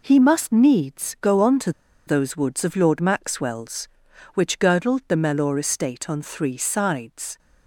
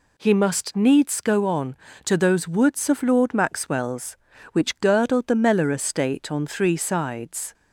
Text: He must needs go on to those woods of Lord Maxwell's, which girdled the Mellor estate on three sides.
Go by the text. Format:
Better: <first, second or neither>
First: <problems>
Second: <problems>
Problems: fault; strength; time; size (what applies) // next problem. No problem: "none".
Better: second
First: pauses between "to" and "those"; at 1.7 s; 0.36 s long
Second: none